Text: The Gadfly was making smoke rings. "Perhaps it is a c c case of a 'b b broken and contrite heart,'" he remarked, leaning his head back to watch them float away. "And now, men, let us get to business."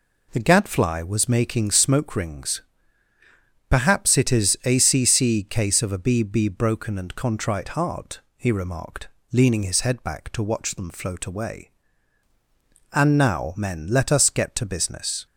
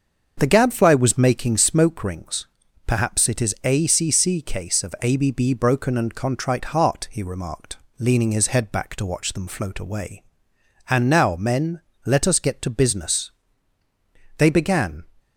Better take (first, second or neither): first